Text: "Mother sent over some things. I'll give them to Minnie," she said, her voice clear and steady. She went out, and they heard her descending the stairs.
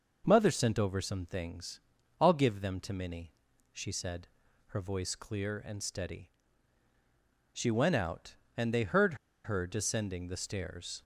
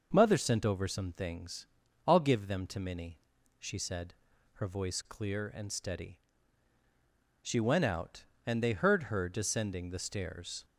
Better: second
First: pauses between "heard" and "her"; slight; at 9.1 s; 0.29 s long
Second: none

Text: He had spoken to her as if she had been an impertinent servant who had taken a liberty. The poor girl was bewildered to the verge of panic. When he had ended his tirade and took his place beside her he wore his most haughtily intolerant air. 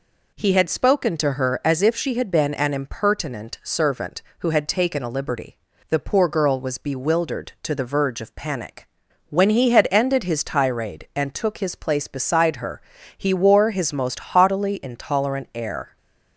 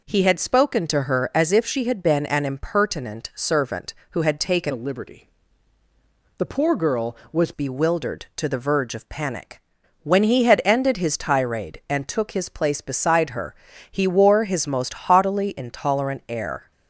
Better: first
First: pauses between "her" and "he"; slight; at 12.8 s; 0.36 s long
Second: changes voice from "a" to "was"; from 4.7 to 7.5 s; 2.8 s long // pauses between "her" and "he"; slight; at 13.5 s; 0.36 s long

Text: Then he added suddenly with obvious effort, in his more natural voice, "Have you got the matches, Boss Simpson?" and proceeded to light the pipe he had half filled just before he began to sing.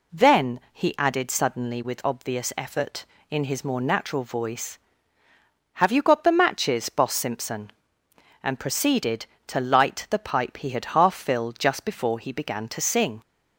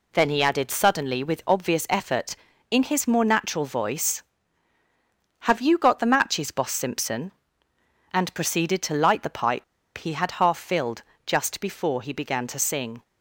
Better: first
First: none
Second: pauses between "pipe" and "he"; slight; at 9.6 s; 0.33 s long // pauses between "filled" and "just"; slight; at 11.0 s; 0.22 s long

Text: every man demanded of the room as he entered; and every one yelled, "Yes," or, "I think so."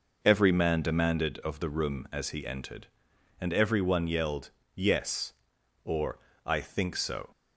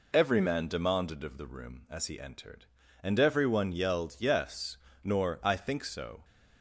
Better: first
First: none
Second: says "nor" for "or"; at 5.0 s

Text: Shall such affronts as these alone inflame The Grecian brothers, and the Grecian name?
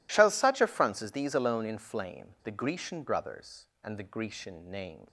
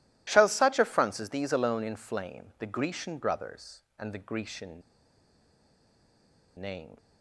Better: first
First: none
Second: pauses between "Grecian" and "name"; strong; at 4.8 s; 1.7 s long

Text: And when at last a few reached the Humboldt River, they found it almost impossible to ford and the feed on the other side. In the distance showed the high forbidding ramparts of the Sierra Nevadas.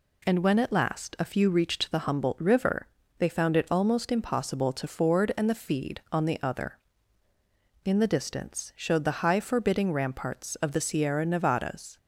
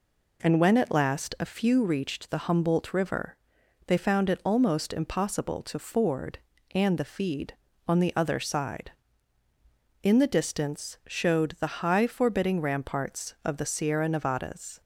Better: second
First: skips "side"; at 7.3 s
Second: none

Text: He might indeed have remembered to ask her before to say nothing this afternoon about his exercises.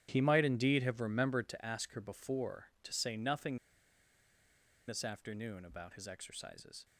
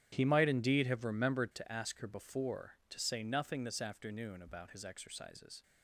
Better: second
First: starts louder than the rest; strong; until 1.1 s; 10 dB // pauses between "nothing" and "this"; strong; at 3.5 s; 1.3 s long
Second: starts louder than the rest; strong; until 1.1 s; 10 dB

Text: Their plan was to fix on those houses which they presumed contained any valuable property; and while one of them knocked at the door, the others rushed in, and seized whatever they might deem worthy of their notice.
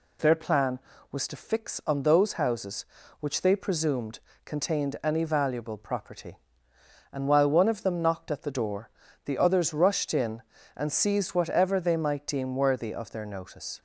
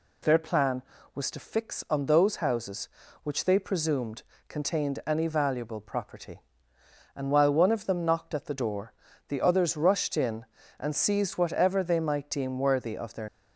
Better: first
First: pauses between "presumed" and "contained"; slight; at 4.1 s; 0.26 s long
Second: pauses between "presumed" and "contained"; slight; at 4.2 s; 0.26 s long // stops before "notice"; at 13.2 s

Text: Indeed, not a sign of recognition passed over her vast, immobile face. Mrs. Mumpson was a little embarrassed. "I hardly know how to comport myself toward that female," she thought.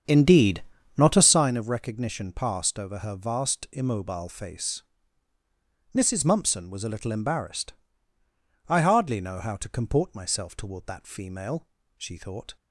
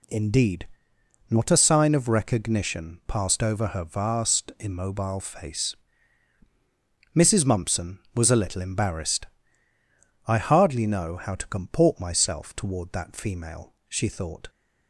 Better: second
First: starts louder than the rest; strong; until 1.5 s; 7.5 dB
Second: none

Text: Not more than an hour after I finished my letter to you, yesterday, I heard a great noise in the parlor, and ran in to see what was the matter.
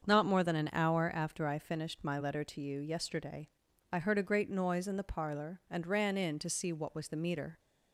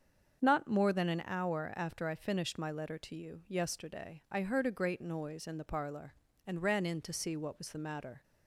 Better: second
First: starts louder than the rest; until 1.0 s; 7 dB // says "meter" for "matter"; at 7.1 s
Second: starts louder than the rest; until 1.4 s; 7 dB

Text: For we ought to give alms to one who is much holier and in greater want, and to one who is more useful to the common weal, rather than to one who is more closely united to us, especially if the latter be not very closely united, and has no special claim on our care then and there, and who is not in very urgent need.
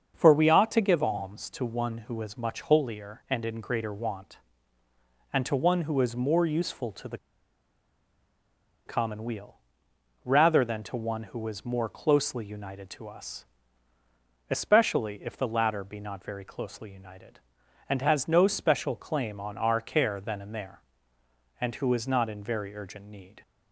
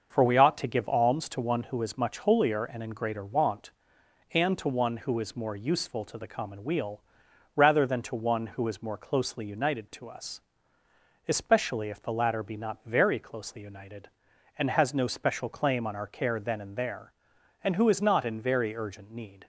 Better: second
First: starts louder than the rest; until 1.1 s; 7 dB // pauses between "the" and "common"; strong; at 7.1 s; 1.6 s long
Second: starts louder than the rest; until 1.1 s; 6.5 dB

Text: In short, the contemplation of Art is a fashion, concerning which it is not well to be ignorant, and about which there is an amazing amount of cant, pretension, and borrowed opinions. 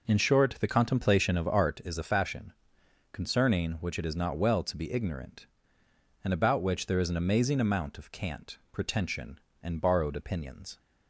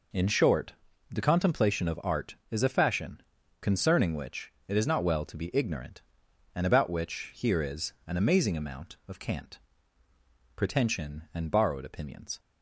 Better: first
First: none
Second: pauses between "which" and "it"; slight; at 4.5 s; 0.16 s long // says "here" for "there"; at 7.3 s // pauses between "is" and "an"; slight; at 7.9 s; 0.16 s long

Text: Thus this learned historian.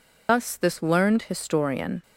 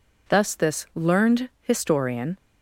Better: second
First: loses the start of "Thus"; at 0.2 s; 90 ms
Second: none

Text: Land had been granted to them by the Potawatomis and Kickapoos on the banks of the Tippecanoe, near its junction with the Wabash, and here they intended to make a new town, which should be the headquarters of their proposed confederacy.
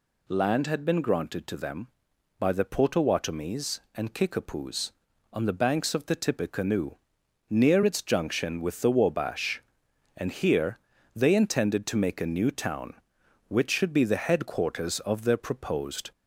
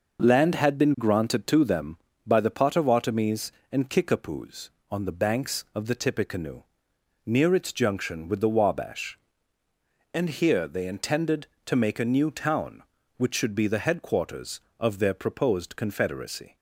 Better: second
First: pauses between "here" and "they"; slight; at 10.7 s; 0.36 s long // stops before "confederacy"; at 16.1 s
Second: none

